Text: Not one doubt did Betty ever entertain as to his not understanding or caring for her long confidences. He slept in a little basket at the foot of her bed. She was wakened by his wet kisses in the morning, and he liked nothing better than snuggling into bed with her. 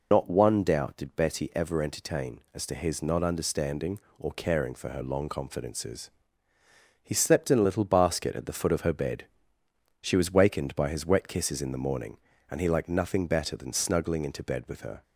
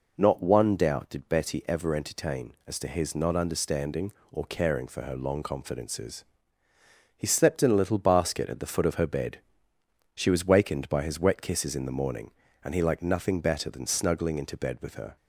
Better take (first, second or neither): second